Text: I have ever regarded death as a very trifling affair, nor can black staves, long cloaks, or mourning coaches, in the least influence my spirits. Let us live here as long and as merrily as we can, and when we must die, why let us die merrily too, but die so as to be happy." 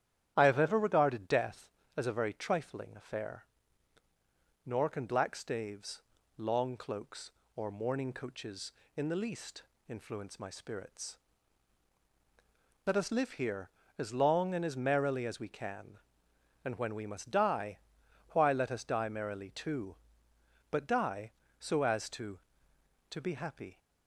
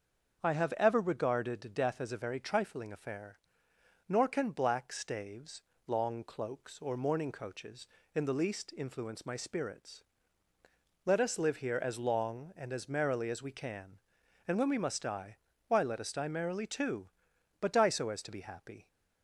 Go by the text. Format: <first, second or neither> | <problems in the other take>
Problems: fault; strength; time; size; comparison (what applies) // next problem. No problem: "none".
second | starts louder than the rest; strong; until 1.3 s; 11 dB; also in the second // pauses between "least" and "influence"; slight; at 9.6 s; 0.26 s long // says "to" twice; at 23.1 s